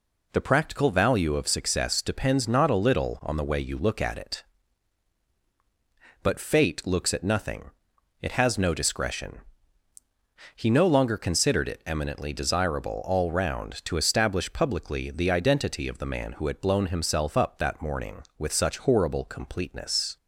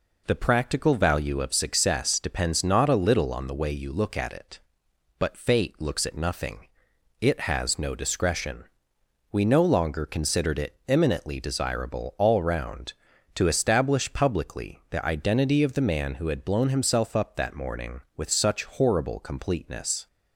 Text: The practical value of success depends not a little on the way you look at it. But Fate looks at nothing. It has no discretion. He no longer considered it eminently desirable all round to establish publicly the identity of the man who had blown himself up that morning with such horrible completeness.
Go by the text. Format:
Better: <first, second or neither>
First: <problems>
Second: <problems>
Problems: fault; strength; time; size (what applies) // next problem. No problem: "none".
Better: first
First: none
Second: says "We" for "He"; at 9.3 s